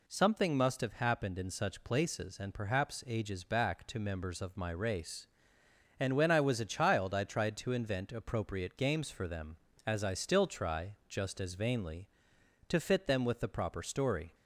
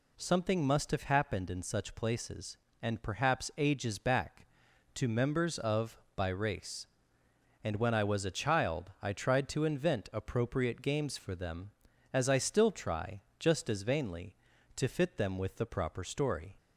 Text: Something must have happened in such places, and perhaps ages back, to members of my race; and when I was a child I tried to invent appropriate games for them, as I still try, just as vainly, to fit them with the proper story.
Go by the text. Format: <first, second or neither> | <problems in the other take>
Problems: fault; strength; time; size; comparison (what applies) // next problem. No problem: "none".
first | says "by" for "my"; at 6.1 s